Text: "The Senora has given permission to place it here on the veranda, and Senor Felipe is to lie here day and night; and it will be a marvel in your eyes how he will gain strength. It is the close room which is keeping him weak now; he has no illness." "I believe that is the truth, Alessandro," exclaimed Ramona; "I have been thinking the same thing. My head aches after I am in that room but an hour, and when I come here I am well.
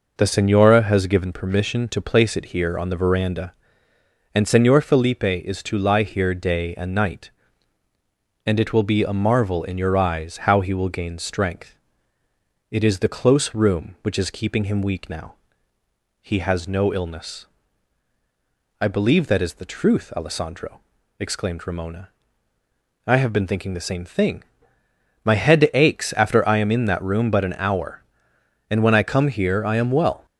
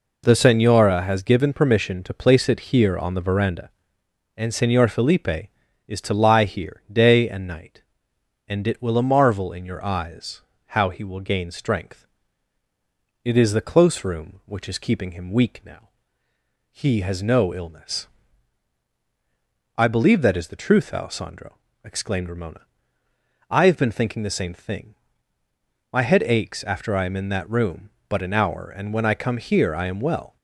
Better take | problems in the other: first | skips "be"; at 8.9 s // pauses between "eyes" and "how"; slight; at 10.4 s; 0.28 s long

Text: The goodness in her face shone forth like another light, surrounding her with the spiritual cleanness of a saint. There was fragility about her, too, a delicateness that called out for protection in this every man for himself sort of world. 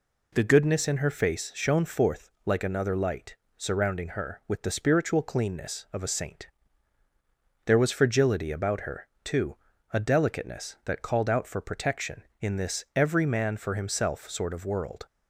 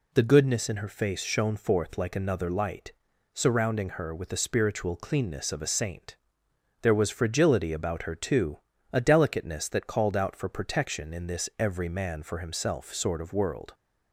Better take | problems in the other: neither | none

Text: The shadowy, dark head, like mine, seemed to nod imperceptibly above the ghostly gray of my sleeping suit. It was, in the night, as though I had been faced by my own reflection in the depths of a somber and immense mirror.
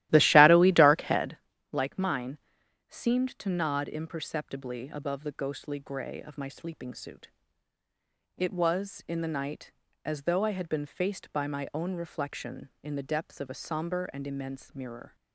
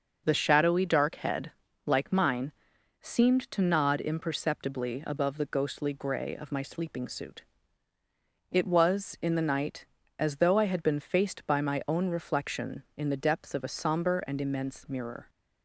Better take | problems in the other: second | starts louder than the rest; strong; until 1.4 s; 15 dB

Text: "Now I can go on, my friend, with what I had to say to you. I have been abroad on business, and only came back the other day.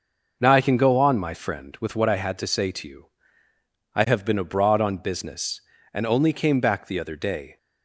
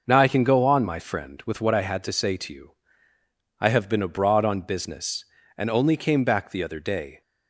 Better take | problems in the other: neither | none

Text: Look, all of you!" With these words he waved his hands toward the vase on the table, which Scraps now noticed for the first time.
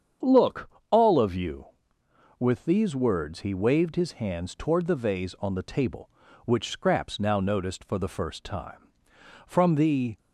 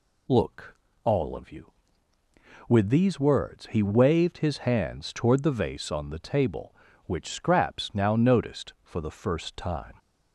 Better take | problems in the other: second | starts louder than the rest; strong; until 1.4 s; 7.5 dB // goes on to say "From the"; noticeable; from 9.4 s on; 0.70 s long

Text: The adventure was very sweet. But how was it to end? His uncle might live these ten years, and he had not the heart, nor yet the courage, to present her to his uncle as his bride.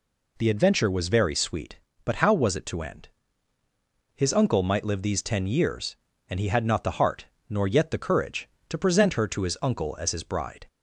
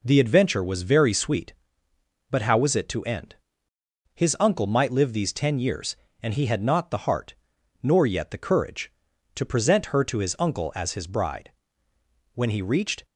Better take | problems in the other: first | goes on to say "When he reached"; noticeable; from 12.3 s on; 0.70 s long

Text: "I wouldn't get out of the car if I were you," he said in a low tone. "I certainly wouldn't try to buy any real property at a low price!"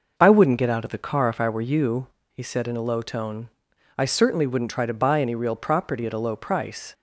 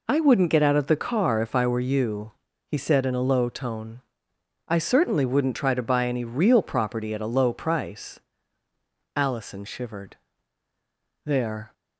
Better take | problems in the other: first | goes on to say "Allison shivered There"; strong; from 9.1 s on; 2.5 s long

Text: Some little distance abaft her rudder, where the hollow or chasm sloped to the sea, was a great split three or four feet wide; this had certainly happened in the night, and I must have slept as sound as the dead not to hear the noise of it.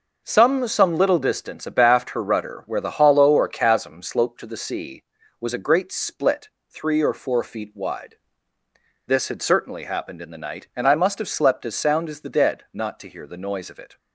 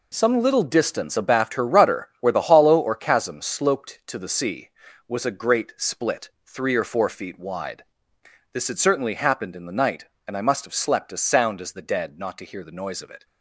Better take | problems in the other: second | says "Some" twice; at 0.6 s // pauses between "split" and "three"; slight; at 6.4 s; 0.22 s long; slight in the second

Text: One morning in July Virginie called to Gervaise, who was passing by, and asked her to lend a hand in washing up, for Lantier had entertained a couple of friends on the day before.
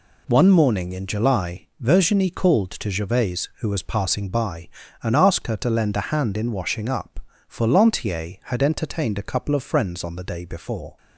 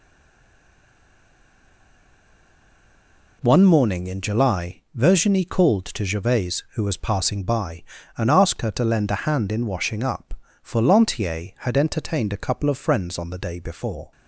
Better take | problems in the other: first | stays silent before the first word; strong; until 3.4 s; 3.4 s long

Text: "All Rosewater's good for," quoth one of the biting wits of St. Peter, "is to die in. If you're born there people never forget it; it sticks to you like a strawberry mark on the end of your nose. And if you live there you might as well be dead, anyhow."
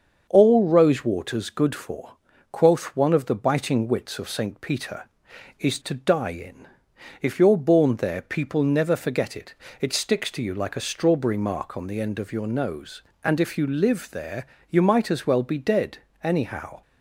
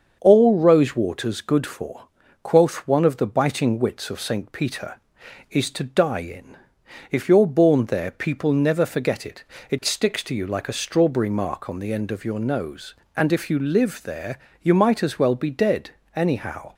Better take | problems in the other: neither | starts louder than the rest; the same in both // pauses between "there" and "you"; slight; the same in both

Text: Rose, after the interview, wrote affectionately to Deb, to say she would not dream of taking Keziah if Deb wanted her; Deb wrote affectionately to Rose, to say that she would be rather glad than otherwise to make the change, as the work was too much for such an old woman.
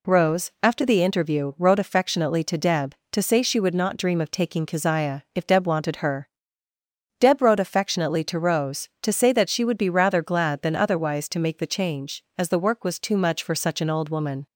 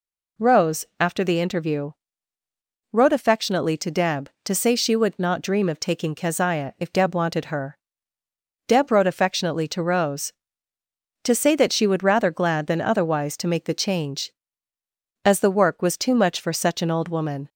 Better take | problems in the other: first | skips "be"; at 12.0 s

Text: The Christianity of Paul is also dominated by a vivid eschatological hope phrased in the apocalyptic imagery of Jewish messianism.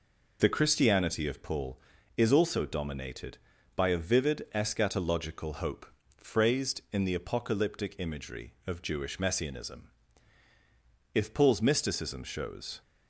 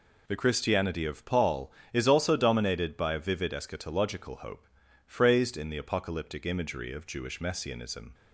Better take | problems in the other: second | pauses between "hope" and "phrased"; slight; at 5.8 s; 0.34 s long; also in the second // goes on to say "If Paul's mysticism shows"; strong; from 11.1 s on; 1.6 s long

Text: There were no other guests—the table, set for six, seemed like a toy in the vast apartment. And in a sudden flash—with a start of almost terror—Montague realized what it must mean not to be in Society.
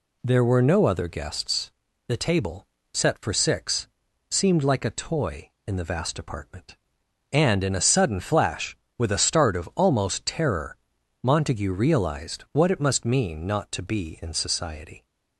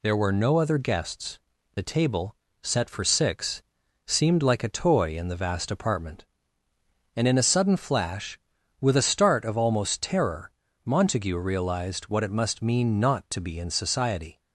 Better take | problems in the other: neither | none

